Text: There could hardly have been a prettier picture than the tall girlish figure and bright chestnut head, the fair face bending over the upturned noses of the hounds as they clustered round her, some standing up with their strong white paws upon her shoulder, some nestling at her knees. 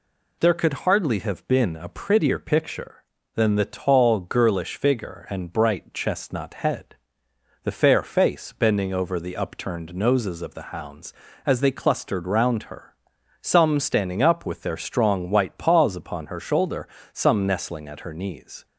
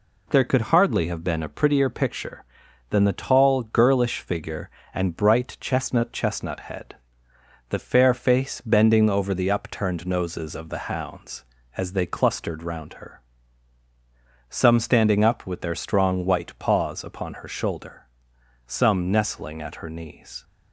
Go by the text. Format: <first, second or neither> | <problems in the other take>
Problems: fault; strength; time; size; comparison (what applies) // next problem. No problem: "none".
first | says "chestnut" twice; at 6.1 s